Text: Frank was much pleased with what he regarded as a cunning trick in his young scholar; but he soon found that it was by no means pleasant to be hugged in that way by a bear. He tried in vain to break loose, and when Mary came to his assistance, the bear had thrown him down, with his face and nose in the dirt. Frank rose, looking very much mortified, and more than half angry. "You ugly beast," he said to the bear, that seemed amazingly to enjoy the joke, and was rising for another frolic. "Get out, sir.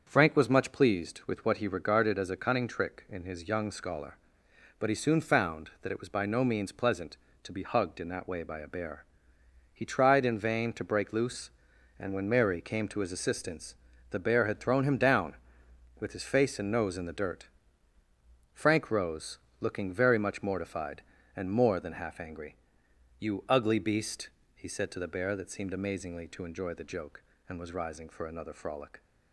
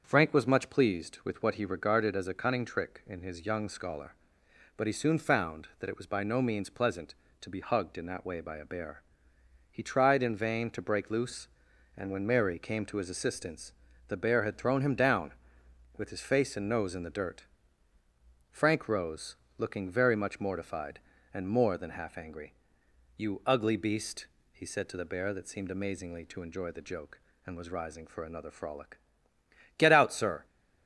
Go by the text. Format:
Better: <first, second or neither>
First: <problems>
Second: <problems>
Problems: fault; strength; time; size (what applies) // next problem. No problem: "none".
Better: second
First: starts louder than the rest; until 1.0 s; 7 dB // stops before "Get out sir"; at 29.0 s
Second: starts louder than the rest; until 1.0 s; 7 dB